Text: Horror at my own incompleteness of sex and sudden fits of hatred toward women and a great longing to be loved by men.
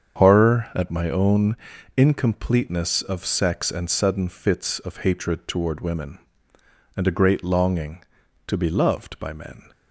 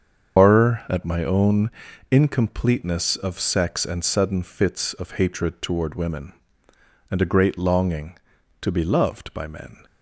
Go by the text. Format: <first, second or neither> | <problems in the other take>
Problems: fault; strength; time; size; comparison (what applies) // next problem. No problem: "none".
first | loses the start of "Horror"; at 0.3 s; 65 ms // starts louder than the rest; strong; until 1.4 s; 7 dB; strong in the first // pauses between "own" and "incompleteness"; at 1.7 s; 0.38 s long; also in the first